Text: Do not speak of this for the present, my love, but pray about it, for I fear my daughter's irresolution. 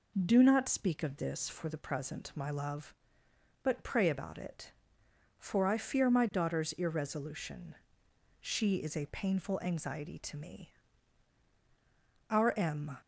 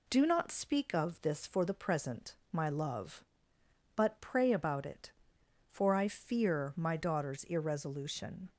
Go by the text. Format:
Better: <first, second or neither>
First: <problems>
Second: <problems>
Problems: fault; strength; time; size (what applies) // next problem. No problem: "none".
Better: second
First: goes on to say "She is a painful anxiety to me Our M"; strong; from 8.3 s on; 4.6 s long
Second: none